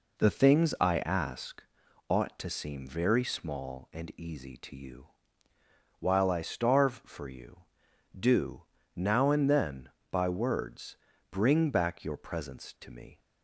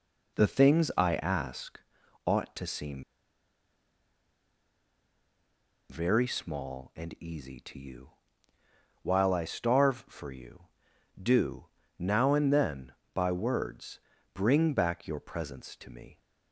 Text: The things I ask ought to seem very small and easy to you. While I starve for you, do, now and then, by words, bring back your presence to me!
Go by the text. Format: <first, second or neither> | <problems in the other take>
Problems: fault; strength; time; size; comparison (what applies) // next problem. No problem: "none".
first | pauses between "ask" and "ought"; noticeable; at 1.7 s; 0.46 s long; noticeable in the first // pauses between "seem" and "very"; strong; at 3.0 s; 2.8 s long